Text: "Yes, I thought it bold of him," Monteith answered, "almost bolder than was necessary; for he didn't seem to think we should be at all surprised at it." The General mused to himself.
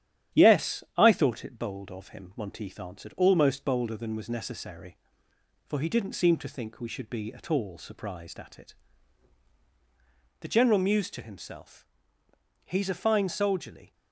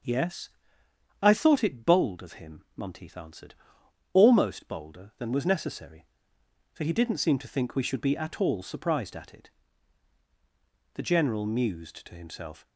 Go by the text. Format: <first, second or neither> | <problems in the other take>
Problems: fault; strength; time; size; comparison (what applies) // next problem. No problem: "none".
second | starts louder than the rest; strong; until 1.4 s; 10.5 dB; also in the second // goes on to say "He's a fine soldierly"; noticeable; from 12.6 s on; 1.2 s long